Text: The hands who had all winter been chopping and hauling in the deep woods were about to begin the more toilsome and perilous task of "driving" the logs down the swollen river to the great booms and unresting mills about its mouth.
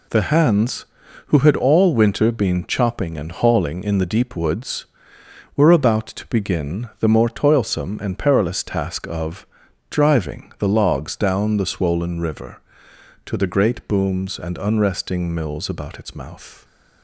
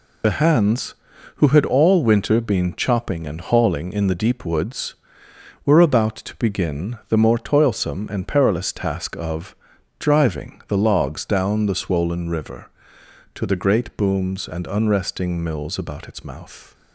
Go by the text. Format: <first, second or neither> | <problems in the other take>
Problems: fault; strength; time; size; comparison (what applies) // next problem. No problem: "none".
first | loses the start of "The"; at 0.2 s; 50 ms // pauses between "of" and "driving"; noticeable; at 9.5 s; 0.46 s long; noticeable in the first